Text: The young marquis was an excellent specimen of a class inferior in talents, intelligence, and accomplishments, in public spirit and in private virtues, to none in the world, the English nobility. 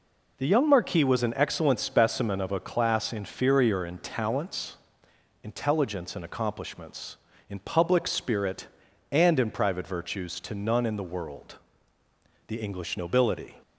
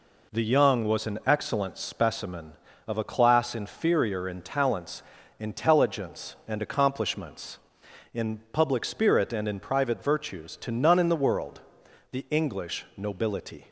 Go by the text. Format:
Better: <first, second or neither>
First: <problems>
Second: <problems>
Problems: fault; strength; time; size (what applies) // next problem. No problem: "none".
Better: first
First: none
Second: skips "marquis"; at 0.8 s